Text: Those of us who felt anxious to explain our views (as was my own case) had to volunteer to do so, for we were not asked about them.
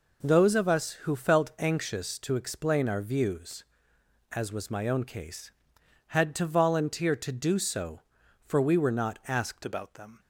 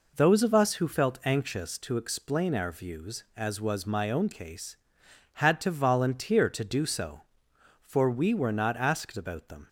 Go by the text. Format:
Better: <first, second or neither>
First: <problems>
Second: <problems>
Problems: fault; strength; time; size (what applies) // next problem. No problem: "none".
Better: second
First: changes voice at "about"; from 9.6 s on; 0.5 s long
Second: none